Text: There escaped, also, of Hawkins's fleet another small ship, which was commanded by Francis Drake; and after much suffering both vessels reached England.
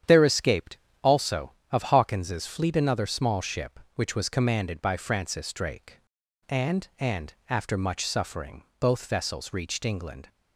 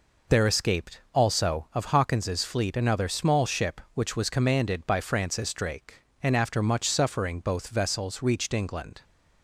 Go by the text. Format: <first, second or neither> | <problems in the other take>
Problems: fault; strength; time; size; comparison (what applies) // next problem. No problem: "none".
second | starts louder than the rest; strong; until 1.3 s; 9 dB // says "and" twice; at 6.9 s // pauses between "suffering" and "both"; slight; at 8.6 s; 0.16 s long